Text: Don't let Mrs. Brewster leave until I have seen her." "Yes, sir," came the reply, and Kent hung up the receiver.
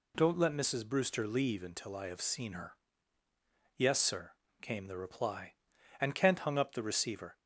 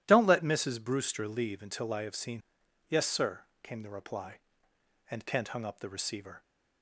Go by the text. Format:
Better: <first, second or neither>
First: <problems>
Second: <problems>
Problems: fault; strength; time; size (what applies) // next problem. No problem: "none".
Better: first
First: none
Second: starts louder than the rest; strong; until 1.0 s; 12.5 dB // skips "her"; at 2.6 s